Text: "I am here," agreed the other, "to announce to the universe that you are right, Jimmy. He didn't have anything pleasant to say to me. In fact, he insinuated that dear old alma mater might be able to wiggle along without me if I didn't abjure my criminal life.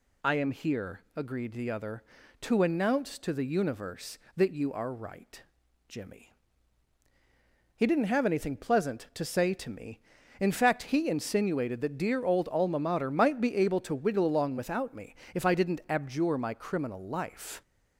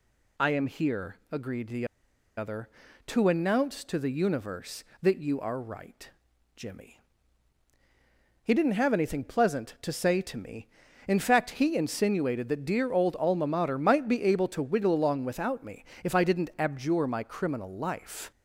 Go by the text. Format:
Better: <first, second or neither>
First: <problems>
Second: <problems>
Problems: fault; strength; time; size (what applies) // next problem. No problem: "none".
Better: first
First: pauses between "me" and "if"; slight; at 15.1 s; 0.18 s long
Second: pauses between "the" and "other"; noticeable; at 1.8 s; 0.50 s long // pauses between "me" and "if"; slight; at 15.8 s; 0.18 s long